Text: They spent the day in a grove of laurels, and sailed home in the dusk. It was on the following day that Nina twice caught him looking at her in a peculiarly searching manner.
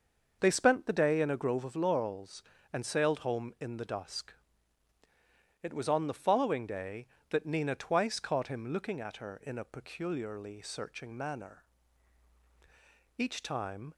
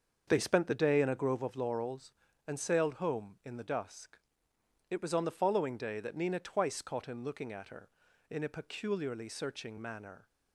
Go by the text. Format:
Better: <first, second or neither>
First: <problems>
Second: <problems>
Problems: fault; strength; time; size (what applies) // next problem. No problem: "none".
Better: second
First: starts louder than the rest; until 1.4 s; 6 dB // goes on to say "Each time"; noticeable; from 13.1 s on; 0.76 s long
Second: starts louder than the rest; until 1.2 s; 6.5 dB